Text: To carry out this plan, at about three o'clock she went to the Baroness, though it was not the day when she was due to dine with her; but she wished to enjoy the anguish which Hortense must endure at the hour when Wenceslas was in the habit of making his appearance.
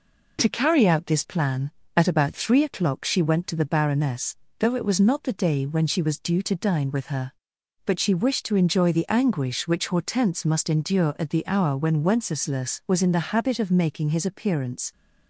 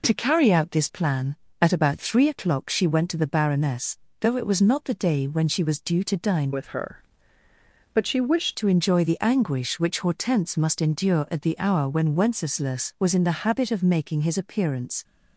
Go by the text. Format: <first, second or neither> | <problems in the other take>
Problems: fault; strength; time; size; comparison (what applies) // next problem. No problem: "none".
first | changes voice from "with" to "wished"; from 6.5 to 8.5 s; 2.0 s long